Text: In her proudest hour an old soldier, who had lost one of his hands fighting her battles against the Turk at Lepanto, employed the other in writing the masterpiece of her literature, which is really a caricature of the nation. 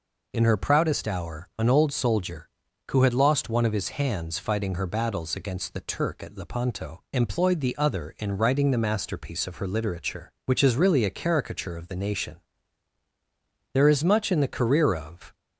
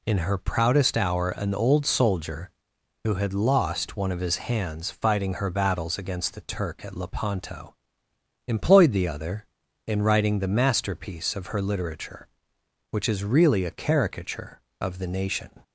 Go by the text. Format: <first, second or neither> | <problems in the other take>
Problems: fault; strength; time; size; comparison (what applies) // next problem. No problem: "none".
second | goes on to say "There is much in the career of"; from 13.7 s on; 1.6 s long